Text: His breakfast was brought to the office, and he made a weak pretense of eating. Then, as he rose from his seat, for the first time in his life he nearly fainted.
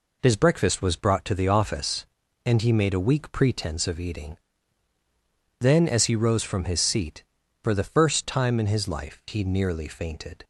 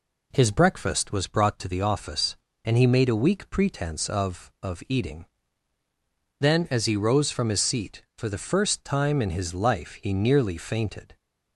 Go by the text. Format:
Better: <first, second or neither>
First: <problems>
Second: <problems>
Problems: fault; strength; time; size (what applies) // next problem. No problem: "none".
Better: first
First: none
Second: says "of" twice; at 4.6 s